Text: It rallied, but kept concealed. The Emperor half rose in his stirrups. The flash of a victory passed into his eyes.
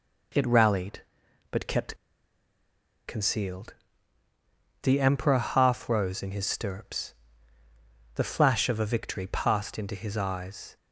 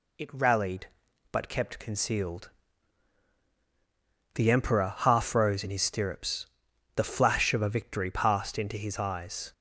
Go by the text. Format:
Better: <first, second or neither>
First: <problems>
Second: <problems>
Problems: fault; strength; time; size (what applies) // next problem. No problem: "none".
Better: second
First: pauses between "kept" and "concealed"; at 1.9 s; 1.1 s long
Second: none